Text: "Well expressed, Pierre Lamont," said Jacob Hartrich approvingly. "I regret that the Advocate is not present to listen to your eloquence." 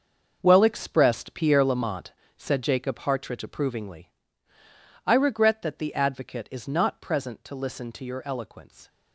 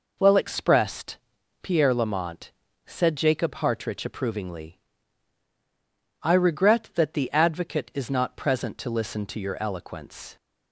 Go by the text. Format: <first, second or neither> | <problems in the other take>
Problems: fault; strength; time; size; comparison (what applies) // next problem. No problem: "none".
second | gets quieter; strong; throughout; 11 dB